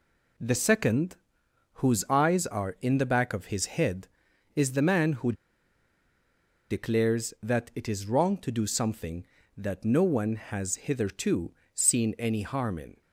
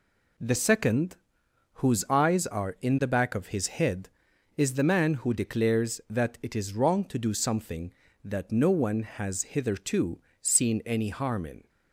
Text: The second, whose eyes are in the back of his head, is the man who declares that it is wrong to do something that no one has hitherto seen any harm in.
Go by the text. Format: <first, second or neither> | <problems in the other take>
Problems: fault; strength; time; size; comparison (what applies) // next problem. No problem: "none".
second | pauses between "who" and "declares"; strong; at 5.3 s; 1.3 s long // pauses between "hitherto" and "seen"; slight; at 11.5 s; 0.22 s long; slight in the second